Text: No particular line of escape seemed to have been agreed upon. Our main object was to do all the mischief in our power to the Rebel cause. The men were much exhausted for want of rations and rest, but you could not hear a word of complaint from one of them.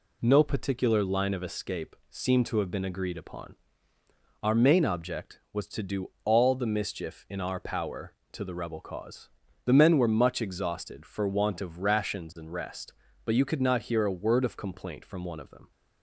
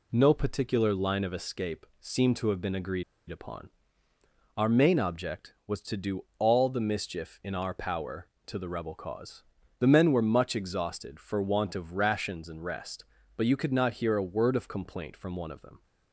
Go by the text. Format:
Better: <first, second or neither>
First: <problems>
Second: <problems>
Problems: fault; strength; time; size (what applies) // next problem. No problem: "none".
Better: first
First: pauses between "escape" and "seemed"; slight; at 1.9 s; 0.16 s long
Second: pauses between "escape" and "seemed"; slight; at 1.8 s; 0.16 s long // pauses between "agreed" and "upon"; slight; at 3.0 s; 0.26 s long